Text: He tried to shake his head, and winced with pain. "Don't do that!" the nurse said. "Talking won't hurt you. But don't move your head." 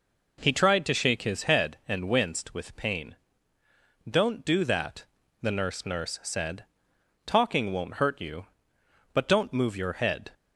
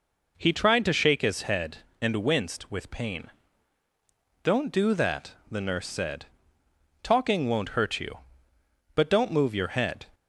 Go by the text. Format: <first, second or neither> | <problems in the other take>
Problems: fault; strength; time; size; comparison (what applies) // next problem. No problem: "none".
second | says "nurse" twice; at 5.8 s